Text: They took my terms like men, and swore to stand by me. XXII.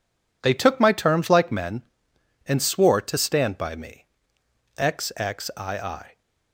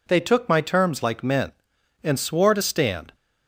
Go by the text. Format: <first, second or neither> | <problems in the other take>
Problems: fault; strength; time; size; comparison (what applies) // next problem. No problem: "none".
first | stops before "by me XXII"; at 3.1 s